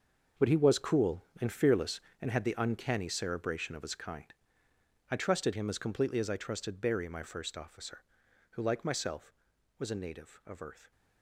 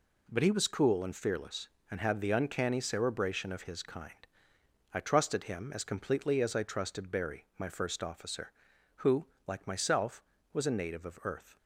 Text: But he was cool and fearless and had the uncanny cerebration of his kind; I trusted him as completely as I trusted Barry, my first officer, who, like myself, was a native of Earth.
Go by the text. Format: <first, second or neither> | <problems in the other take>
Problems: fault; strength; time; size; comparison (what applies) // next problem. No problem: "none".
second | gets quieter; strong; throughout; 13 dB